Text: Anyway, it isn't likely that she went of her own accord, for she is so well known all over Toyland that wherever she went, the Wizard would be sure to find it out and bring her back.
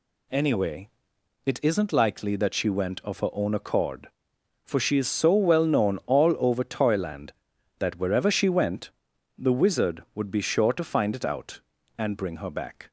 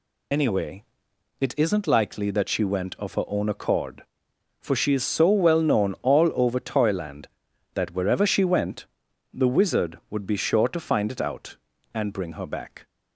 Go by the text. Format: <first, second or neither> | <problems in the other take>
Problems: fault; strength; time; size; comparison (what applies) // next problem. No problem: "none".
first | loses the start of "Anyway"; at 0.3 s; 60 ms